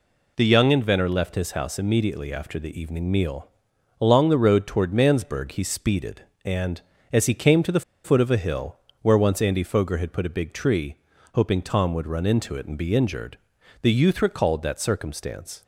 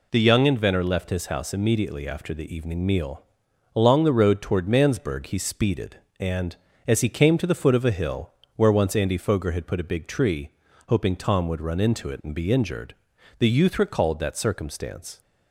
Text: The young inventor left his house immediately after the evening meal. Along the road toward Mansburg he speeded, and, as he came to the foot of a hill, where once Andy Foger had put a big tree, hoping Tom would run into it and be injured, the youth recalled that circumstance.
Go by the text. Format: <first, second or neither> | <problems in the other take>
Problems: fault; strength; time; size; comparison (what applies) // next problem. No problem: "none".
second | pauses between "the" and "foot"; slight; at 7.8 s; 0.23 s long